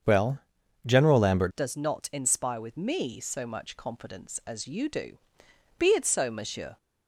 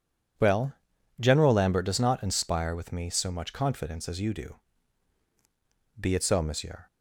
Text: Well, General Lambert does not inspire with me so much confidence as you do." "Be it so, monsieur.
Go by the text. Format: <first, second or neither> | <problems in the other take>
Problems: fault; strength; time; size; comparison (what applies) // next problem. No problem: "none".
second | starts louder than the rest; strong; until 1.4 s; 8.5 dB // changes voice at "does"; from 1.5 s on; 5.2 s long